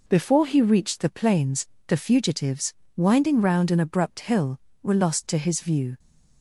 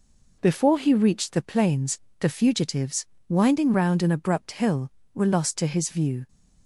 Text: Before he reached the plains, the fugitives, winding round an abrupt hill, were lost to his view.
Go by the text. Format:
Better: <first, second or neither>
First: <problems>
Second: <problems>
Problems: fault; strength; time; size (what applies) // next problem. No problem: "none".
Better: neither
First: none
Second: none